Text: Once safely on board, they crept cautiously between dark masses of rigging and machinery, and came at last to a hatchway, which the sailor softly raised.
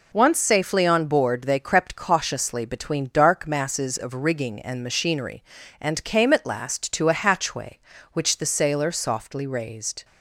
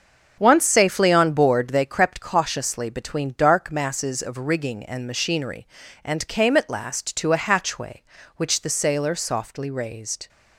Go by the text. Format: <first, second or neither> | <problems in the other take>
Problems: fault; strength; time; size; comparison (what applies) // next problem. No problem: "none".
first | starts louder than the rest; until 1.9 s; 6.5 dB